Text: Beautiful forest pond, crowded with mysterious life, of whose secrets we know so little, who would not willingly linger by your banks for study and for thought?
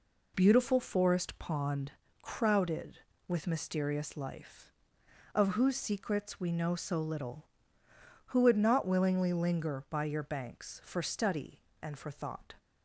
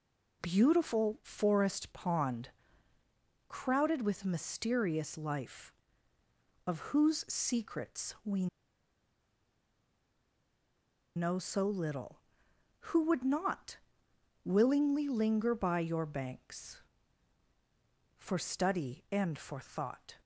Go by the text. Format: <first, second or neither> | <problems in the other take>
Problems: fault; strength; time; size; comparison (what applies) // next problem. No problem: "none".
first | pauses between "we" and "know"; strong; at 8.4 s; 2.6 s long // pauses between "not" and "willingly"; noticeable; at 13.7 s; 0.66 s long